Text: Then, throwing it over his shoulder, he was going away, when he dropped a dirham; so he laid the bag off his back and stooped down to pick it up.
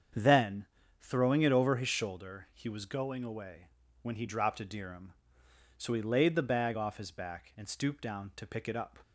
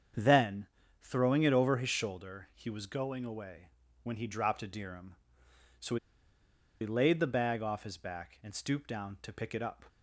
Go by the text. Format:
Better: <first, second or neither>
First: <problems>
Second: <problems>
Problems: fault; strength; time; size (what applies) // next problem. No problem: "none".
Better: first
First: starts louder than the rest; strong; until 1.5 s; 7.5 dB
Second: starts louder than the rest; strong; until 1.5 s; 7.5 dB // pauses between "so" and "he"; noticeable; at 5.9 s; 0.84 s long